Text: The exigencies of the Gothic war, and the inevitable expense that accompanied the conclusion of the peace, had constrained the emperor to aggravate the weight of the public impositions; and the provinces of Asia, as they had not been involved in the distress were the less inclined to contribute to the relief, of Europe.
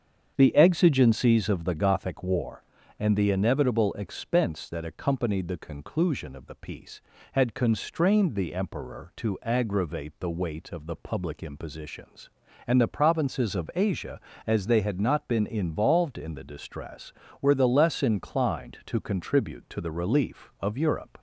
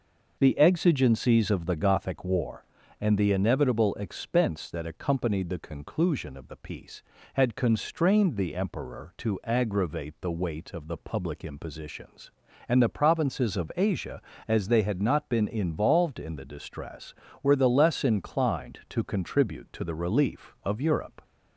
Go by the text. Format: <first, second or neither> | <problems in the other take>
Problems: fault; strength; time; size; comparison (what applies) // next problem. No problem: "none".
second | starts louder than the rest; strong; until 1.3 s; 7.5 dB